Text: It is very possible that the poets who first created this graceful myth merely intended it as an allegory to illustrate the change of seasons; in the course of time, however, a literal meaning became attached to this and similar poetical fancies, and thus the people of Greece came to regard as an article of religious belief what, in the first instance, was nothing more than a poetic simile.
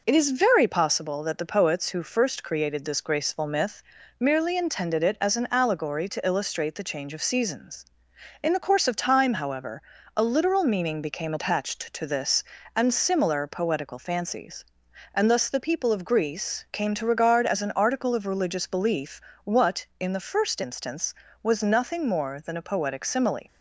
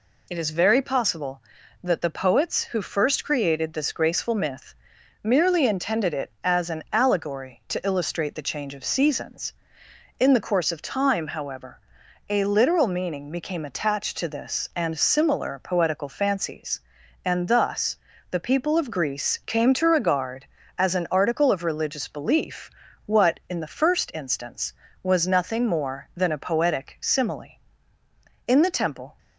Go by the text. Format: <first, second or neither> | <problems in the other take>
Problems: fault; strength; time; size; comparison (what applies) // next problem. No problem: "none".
first | pauses between "myth" and "merely"; noticeable; at 4.7 s; 0.48 s long; also in the first // pauses between "thus" and "the"; slight; at 17.9 s; 0.32 s long // pauses between "belief" and "what"; slight; at 22.6 s; 0.36 s long; slight in the first // goes on to say "In the temple"; noticeable; from 28.4 s on; 0.70 s long